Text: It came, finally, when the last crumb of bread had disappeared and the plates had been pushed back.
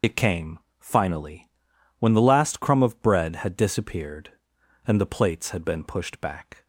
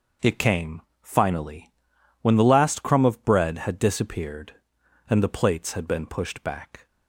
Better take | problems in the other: second | loses the start of "It"; at 0.0 s; 50 ms

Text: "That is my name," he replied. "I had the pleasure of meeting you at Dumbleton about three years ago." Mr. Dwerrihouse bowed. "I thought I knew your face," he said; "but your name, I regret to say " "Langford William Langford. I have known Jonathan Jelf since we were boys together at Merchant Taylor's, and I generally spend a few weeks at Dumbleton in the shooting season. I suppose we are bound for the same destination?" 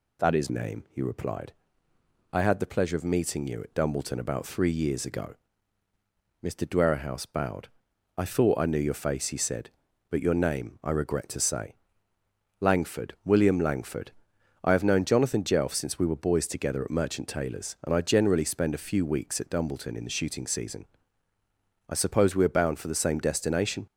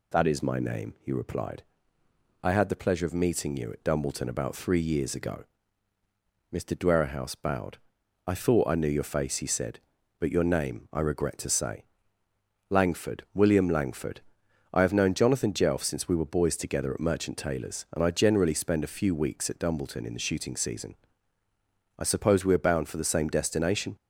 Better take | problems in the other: second | skips "my"; at 0.4 s

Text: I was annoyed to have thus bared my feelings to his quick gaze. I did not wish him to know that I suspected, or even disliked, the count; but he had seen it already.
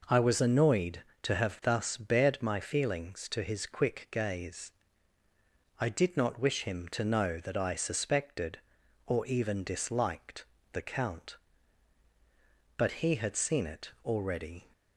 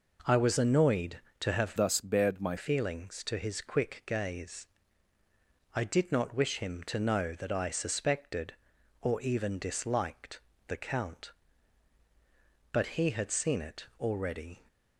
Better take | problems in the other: first | changes voice from "thus" to "my"; from 1.7 to 2.5 s; 0.8 s long

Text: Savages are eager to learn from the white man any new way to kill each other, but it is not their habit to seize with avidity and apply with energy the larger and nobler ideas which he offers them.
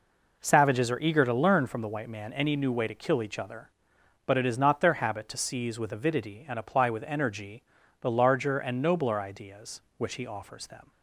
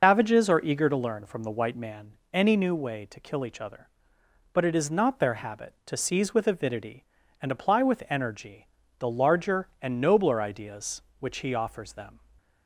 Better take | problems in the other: first | loses the start of "Savages"; at 0.0 s; 135 ms // pauses between "man" and "any"; slight; at 2.1 s; 0.16 s long // pauses between "energy" and "the"; slight; at 8.6 s; 0.32 s long; also in the first

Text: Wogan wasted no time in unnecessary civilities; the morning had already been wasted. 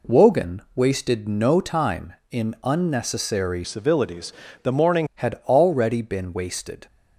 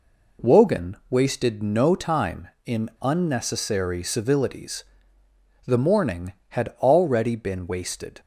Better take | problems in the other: second | changes voice from "civilities" to "morning"; from 3.6 to 5.0 s; 1.4 s long

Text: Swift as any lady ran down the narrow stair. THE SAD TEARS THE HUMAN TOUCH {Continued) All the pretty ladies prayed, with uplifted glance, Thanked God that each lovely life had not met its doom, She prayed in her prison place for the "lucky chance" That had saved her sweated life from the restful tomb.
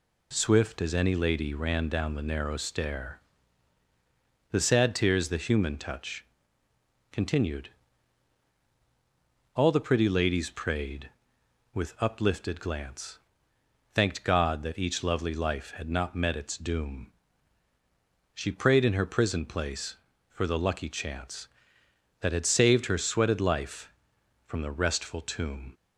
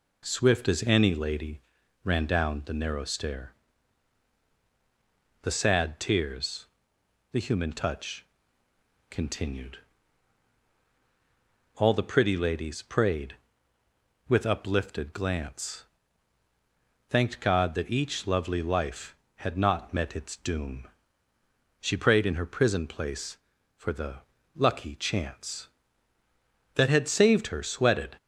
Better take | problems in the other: first | pauses between "lady" and "ran"; at 1.5 s; 0.42 s long // pauses between "TEARS" and "THE"; noticeable; at 6.6 s; 0.68 s long // pauses between "the" and "lucky"; slight; at 24.1 s; 0.36 s long // stops before "life from the restful tomb"; at 28.1 s

